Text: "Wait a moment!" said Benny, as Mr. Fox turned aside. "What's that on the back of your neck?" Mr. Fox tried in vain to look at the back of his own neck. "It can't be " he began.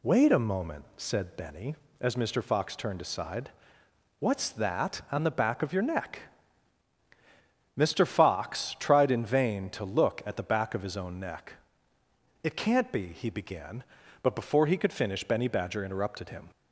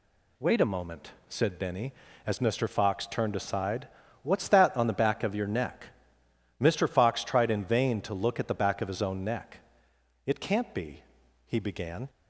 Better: second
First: goes on to say "But before he could finish Benny Badger interrupted him"; strong; from 14.2 s on; 2.2 s long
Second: none

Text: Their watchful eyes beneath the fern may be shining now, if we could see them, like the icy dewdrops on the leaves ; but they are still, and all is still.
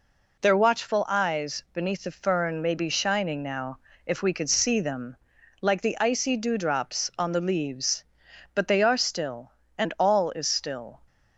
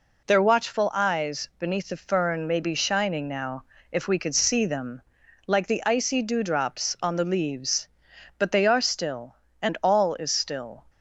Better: neither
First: none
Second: none

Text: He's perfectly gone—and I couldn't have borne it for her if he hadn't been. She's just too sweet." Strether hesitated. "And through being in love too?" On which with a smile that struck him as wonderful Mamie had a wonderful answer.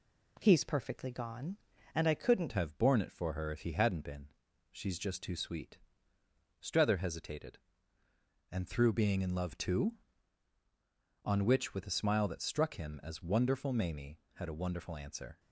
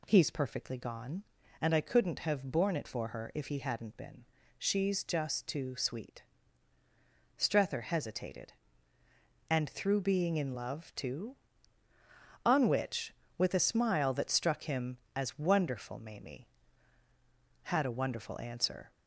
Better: second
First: changes voice at "have"; from 2.5 s on; 12.8 s long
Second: none

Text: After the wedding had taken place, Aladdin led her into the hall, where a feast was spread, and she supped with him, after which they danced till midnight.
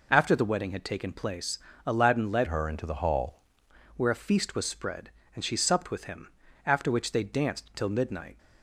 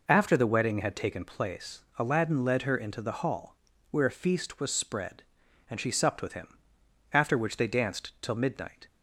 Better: second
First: changes voice from "her" to "hall"; from 2.4 to 3.3 s; 0.9 s long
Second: none

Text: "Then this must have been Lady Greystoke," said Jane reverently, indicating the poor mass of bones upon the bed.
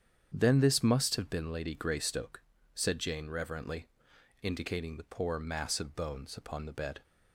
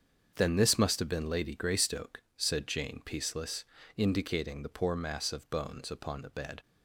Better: first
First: starts louder than the rest; strong; until 1.3 s; 8 dB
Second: starts louder than the rest; until 1.3 s; 7 dB // says "peaceless" for "reverently"; at 3.0 s

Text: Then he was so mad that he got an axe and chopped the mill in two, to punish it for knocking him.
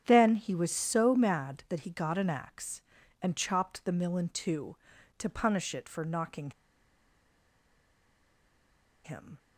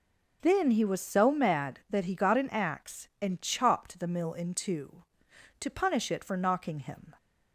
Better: second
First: starts louder than the rest; strong; until 1.0 s; 8.5 dB // pauses between "knocking" and "him"; strong; at 6.5 s; 2.5 s long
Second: none

